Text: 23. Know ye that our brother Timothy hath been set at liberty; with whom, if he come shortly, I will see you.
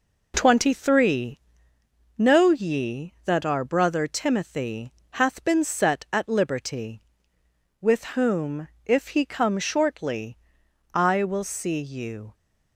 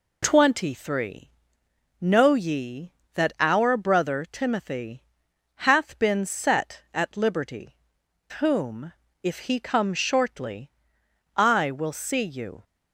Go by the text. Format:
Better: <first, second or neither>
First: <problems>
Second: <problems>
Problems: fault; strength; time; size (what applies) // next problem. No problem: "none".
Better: first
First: pauses between "Timothy" and "hath"; slight; at 4.9 s; 0.22 s long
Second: pauses between "Timothy" and "hath"; noticeable; at 5.0 s; 0.64 s long // skips "with"; at 8.0 s